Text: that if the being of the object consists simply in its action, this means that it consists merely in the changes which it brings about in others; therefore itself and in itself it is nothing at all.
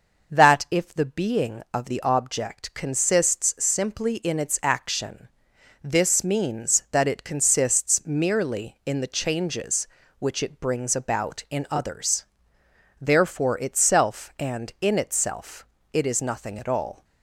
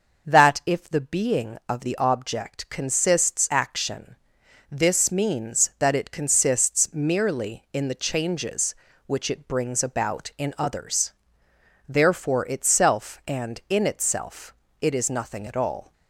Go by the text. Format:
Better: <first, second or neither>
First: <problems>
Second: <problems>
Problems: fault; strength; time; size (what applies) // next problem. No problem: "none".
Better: first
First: pauses between "itself" and "it"; slight; at 15.6 s; 0.26 s long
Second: skips "simply in its"; at 3.4 s // pauses between "itself" and "it"; slight; at 14.5 s; 0.26 s long